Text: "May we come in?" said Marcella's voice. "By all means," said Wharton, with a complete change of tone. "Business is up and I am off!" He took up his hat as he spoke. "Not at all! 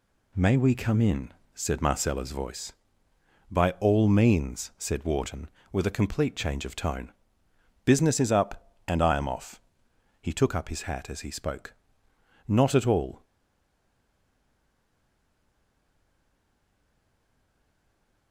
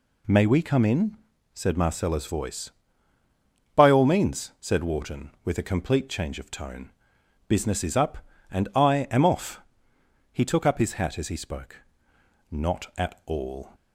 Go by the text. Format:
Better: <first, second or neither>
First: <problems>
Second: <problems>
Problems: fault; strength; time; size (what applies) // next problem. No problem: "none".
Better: second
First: stays silent after the last word; strong; from 13.2 s on; 5.1 s long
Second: none